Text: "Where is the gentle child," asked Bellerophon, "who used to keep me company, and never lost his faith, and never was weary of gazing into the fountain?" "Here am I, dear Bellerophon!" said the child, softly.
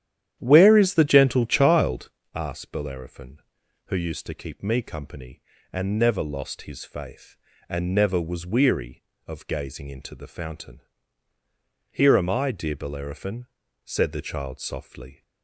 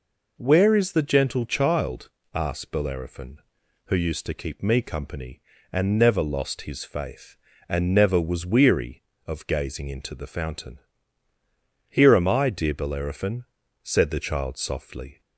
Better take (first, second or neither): second